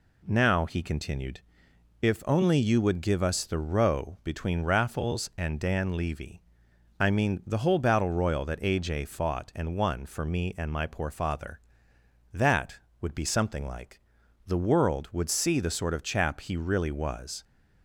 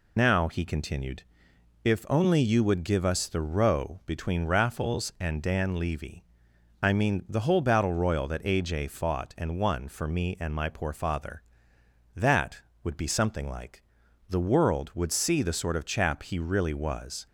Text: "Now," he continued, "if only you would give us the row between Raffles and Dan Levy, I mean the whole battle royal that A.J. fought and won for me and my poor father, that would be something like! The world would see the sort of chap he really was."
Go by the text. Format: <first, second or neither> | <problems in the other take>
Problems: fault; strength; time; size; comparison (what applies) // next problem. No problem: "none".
first | loses the start of "Now"; at 0.1 s; 95 ms